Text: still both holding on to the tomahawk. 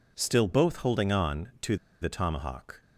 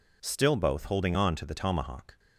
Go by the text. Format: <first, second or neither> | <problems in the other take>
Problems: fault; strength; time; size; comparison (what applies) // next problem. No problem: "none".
second | pauses between "to" and "the"; slight; at 1.7 s; 0.26 s long